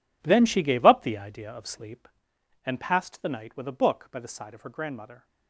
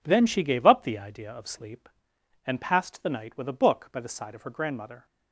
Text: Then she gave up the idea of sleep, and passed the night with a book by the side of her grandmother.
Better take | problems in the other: second | gets quieter; strong; throughout; 14 dB

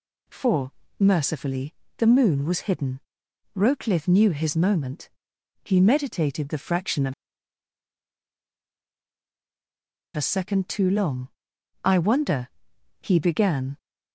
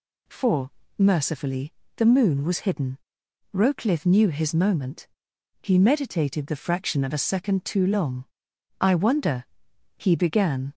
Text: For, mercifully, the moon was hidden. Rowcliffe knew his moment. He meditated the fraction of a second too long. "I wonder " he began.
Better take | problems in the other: second | pauses between "of" and "a"; strong; at 7.1 s; 3.0 s long

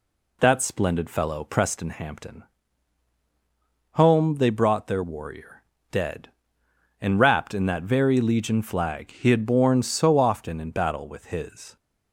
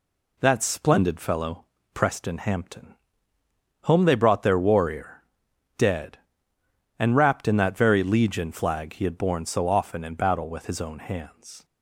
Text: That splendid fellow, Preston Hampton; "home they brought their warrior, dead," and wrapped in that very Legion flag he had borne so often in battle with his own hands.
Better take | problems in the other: second | stops before "own hands"; at 11.7 s

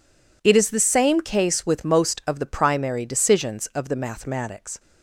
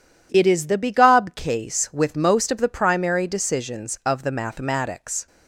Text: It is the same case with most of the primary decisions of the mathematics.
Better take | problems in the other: first | says "begob" for "same"; at 0.7 s

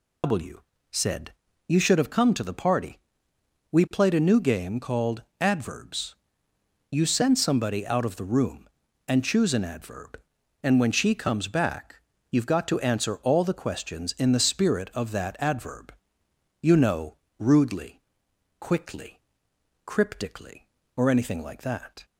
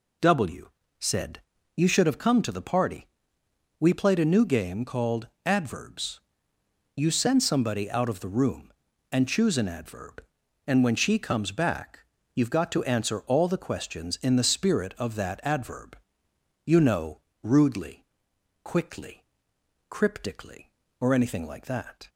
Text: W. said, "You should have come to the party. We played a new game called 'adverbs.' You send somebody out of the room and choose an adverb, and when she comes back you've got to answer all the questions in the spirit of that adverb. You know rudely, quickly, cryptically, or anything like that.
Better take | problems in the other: second | loses the start of "W"; at 0.2 s; 100 ms // pauses between "called" and "adverbs"; slight; at 5.2 s; 0.18 s long; slight in the second // pauses between "back" and "you've"; slight; at 11.9 s; 0.34 s long; slight in the second // pauses between "know" and "rudely"; slight; at 17.1 s; 0.22 s long; slight in the second

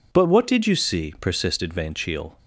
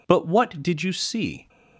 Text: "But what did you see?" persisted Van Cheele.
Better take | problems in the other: first | stops before "persisted Van Cheele"; at 1.4 s

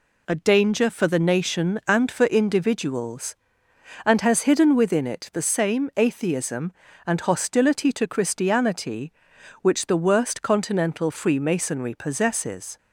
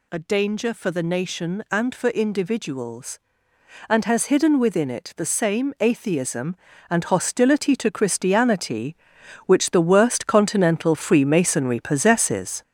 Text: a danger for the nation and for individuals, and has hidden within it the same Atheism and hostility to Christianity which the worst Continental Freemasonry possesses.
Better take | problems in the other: first | gets louder; noticeable; throughout; 6 dB

